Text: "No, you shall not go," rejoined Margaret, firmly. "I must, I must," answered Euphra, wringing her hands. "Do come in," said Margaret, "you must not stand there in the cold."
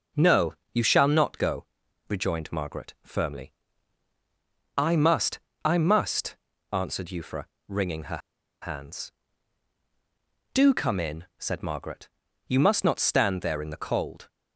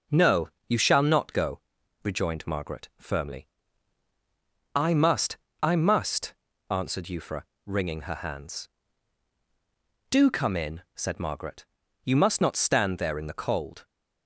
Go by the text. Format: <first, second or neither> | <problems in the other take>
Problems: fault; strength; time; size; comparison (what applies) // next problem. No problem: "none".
second | pauses between "her" and "hands"; at 8.2 s; 0.43 s long